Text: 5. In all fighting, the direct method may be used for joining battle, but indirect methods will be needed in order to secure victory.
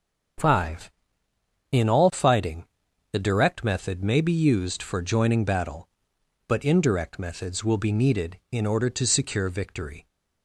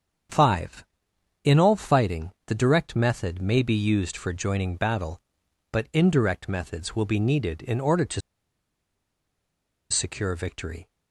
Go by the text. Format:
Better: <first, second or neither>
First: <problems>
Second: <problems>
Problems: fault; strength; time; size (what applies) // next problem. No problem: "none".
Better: first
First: starts louder than the rest; until 2.2 s; 6.5 dB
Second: starts louder than the rest; strong; until 1.8 s; 7.5 dB // pauses between "to" and "secure"; strong; at 8.2 s; 1.7 s long